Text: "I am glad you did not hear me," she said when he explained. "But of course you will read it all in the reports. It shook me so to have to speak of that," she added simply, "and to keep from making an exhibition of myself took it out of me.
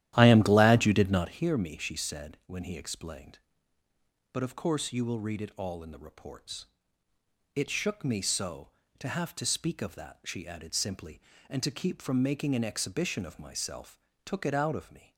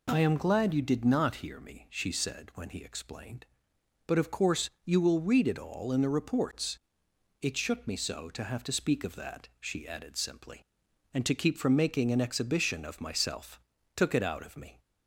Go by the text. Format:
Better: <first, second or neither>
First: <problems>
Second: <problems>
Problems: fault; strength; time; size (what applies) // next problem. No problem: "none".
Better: second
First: starts louder than the rest; strong; until 1.3 s; 12.5 dB // pauses between "myself" and "took"; slight; at 13.9 s; 0.26 s long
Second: pauses between "myself" and "took"; slight; at 13.6 s; 0.34 s long